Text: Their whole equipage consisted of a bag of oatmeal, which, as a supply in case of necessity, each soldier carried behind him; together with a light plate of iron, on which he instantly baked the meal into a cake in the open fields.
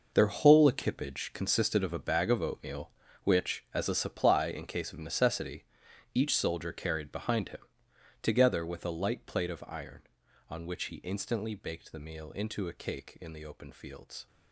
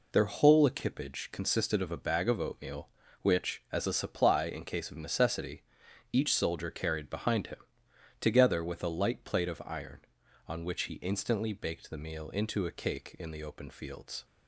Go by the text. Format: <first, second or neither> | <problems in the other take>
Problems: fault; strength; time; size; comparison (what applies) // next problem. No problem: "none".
second | gets quieter; strong; throughout; 12 dB